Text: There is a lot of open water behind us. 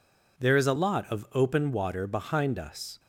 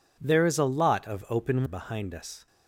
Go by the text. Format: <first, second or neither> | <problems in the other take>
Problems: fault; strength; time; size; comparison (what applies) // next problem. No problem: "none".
first | skips "water"; at 1.6 s